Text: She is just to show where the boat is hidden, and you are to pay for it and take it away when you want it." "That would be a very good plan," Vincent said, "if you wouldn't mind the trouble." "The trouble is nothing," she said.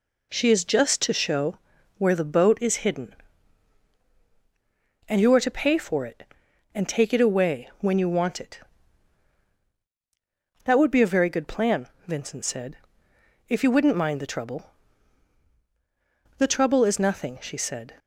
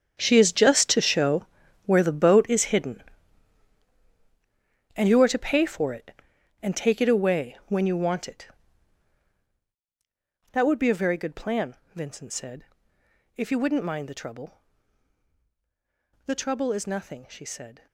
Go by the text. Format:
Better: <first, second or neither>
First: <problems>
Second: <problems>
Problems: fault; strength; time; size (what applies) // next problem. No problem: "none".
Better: first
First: pauses between "show" and "where"; at 1.5 s; 0.40 s long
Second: gets quieter; strong; throughout; 14.5 dB // pauses between "show" and "where"; at 1.4 s; 0.40 s long